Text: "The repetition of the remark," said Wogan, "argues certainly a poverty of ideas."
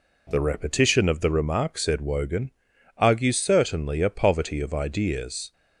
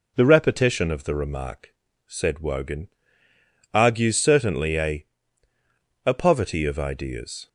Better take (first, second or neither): first